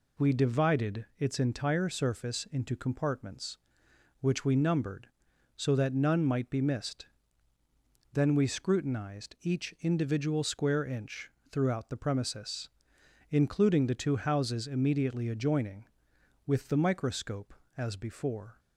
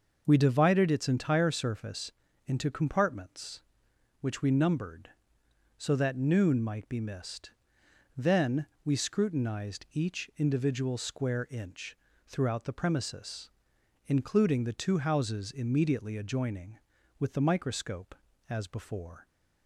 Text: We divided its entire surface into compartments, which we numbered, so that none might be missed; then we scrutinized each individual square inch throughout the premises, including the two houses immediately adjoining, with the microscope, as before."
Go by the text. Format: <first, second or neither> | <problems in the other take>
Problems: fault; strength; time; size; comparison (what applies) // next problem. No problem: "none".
first | pauses between "surface" and "into"; slight; at 2.1 s; 0.36 s long // says "noon" for "none"; at 6.1 s // pauses between "then" and "we"; slight; at 8.6 s; 0.18 s long // pauses between "inch" and "throughout"; slight; at 11.9 s; 0.32 s long; slight in the first